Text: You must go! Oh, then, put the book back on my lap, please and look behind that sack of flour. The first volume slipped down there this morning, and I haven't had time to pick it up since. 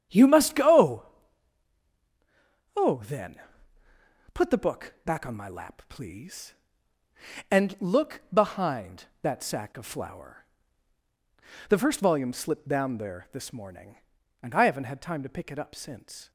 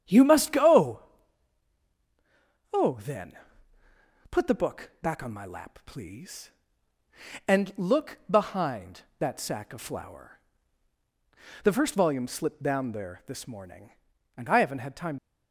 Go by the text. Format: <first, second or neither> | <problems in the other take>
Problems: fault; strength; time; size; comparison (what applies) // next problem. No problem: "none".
first | starts louder than the rest; strong; until 2.7 s; 9 dB; strong in the first // stops before "to pick it up since"; at 15.1 s